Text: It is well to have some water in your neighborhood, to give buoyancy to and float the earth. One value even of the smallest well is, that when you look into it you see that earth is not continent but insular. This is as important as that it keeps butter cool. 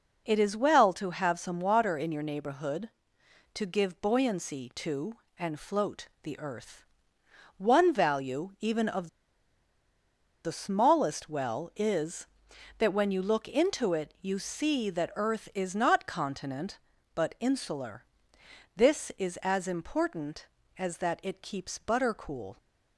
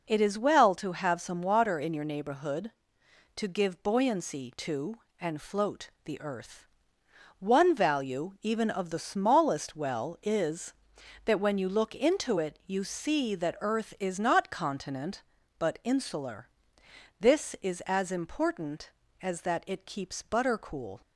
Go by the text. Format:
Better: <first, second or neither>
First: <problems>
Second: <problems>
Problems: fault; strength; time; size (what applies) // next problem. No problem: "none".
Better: second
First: pauses between "float" and "the"; slight; at 6.0 s; 0.16 s long // pauses between "of" and "the"; strong; at 9.0 s; 1.3 s long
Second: pauses between "float" and "the"; slight; at 5.8 s; 0.16 s long